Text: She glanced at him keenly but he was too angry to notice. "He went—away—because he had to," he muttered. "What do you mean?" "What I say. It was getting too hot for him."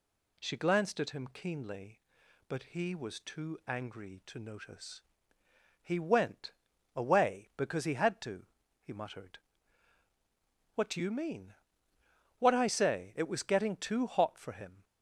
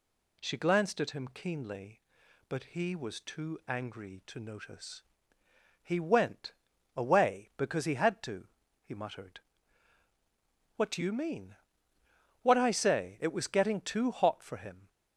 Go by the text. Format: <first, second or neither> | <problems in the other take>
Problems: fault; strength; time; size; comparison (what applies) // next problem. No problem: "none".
neither | none